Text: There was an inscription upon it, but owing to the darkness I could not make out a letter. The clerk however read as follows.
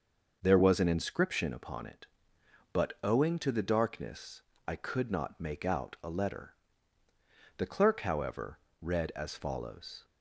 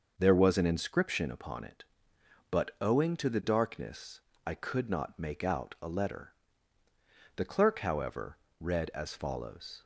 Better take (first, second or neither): neither